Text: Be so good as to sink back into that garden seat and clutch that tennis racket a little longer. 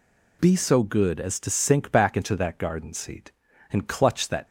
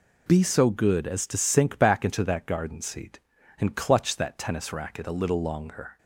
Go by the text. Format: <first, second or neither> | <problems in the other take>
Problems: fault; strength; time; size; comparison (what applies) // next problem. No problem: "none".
second | stops before "tennis racket a little longer"; at 4.4 s